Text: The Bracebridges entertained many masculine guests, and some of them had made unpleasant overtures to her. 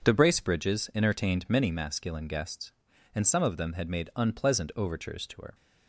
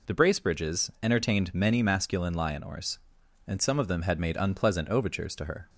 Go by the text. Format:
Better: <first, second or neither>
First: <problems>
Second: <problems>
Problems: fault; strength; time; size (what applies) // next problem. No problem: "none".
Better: first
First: none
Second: says "lionors" for "guests"; at 2.3 s